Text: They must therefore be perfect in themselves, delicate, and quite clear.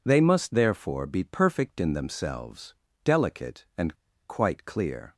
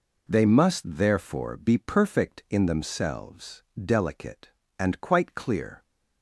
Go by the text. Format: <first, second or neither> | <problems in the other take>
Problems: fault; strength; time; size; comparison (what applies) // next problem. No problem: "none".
second | pauses between "and" and "quite"; slight; at 3.9 s; 0.34 s long